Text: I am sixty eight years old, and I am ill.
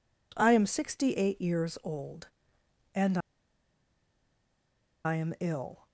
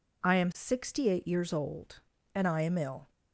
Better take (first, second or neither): second